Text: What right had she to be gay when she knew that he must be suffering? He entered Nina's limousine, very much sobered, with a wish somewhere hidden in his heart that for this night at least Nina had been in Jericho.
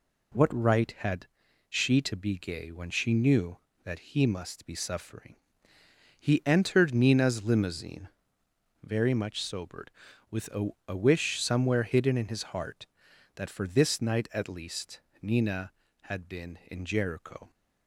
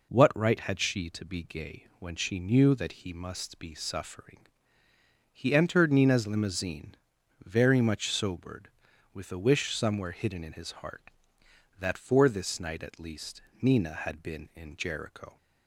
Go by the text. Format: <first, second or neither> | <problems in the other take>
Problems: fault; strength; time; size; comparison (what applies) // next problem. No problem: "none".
second | pauses between "had" and "she"; at 1.2 s; 0.42 s long // says "a" twice; at 10.8 s // pauses between "least" and "Nina"; slight; at 15.0 s; 0.20 s long; slight in the second